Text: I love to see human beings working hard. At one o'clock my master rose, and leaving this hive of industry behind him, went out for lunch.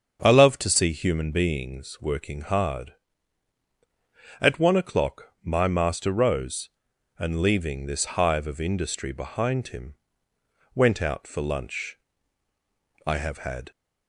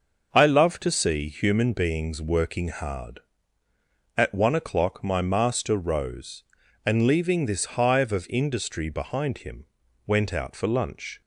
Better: second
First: starts louder than the rest; until 1.2 s; 7 dB // goes on to say "I have had"; noticeable; from 13.0 s on; 0.64 s long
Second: starts louder than the rest; noticeable; until 1.3 s; 6 dB

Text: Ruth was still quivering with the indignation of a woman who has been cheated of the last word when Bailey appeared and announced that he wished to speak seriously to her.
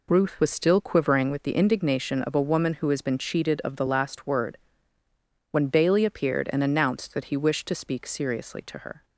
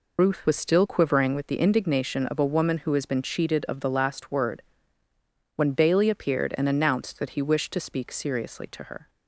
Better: first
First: pauses between "word" and "when"; noticeable; at 4.5 s; 0.94 s long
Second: loses the start of "Ruth"; at 0.1 s; 45 ms // pauses between "word" and "when"; noticeable; at 4.6 s; 0.94 s long

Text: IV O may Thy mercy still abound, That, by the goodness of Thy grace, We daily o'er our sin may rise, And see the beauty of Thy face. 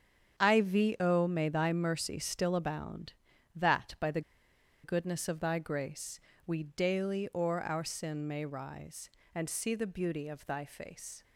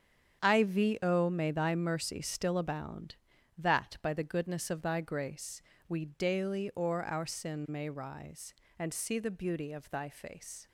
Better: second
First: starts louder than the rest; strong; until 1.4 s; 8 dB // pauses between "the" and "goodness"; noticeable; at 4.2 s; 0.63 s long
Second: starts louder than the rest; strong; until 1.4 s; 8 dB

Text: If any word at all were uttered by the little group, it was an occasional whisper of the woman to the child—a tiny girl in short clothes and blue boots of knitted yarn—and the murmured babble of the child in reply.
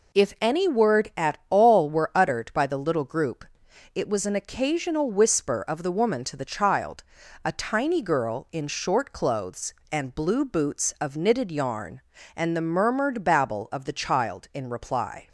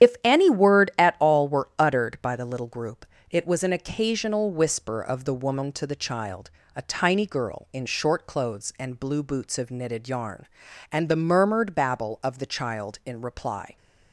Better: first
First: none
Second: loses the start of "If"; at 0.0 s; 55 ms // starts louder than the rest; strong; until 1.2 s; 10 dB

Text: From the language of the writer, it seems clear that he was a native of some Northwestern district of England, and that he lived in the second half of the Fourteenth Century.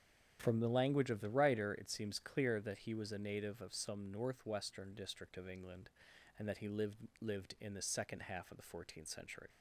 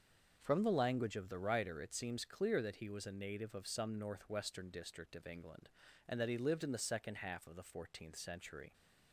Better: second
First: starts louder than the rest; strong; until 1.4 s; 8.5 dB // says "lived" twice; at 7.2 s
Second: starts louder than the rest; until 1.4 s; 6.5 dB

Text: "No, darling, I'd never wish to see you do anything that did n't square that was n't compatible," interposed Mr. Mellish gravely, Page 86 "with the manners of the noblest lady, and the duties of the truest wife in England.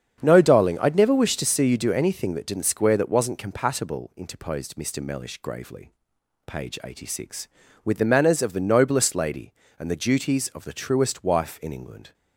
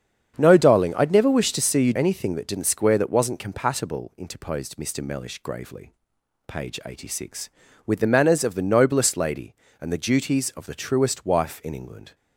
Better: first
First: starts louder than the rest; strong; until 1.2 s; 8 dB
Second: starts louder than the rest; strong; until 1.3 s; 8 dB // skips "do"; at 1.9 s

